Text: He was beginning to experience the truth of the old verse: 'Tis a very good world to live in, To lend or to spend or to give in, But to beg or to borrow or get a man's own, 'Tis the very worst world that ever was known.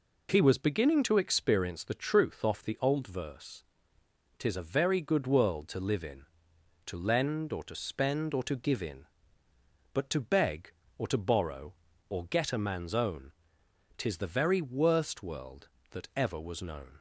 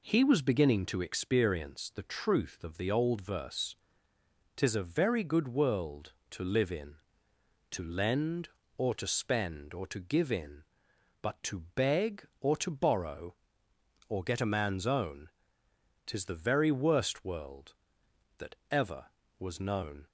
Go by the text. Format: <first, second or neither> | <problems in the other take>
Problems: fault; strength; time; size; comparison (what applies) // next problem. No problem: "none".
second | says "off" for "of"; at 2.4 s